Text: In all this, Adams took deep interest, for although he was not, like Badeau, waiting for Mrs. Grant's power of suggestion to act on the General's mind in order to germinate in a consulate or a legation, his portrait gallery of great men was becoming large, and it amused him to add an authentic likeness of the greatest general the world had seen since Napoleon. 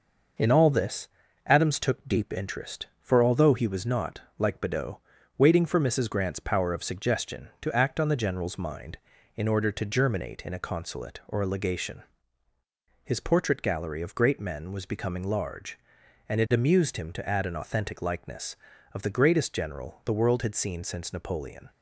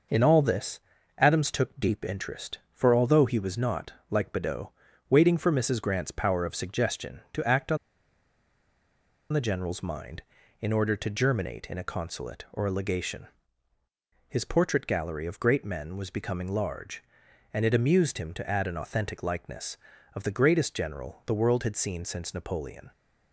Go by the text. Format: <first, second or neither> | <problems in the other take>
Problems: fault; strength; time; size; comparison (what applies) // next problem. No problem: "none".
first | pauses between "on" and "the"; strong; at 7.7 s; 1.5 s long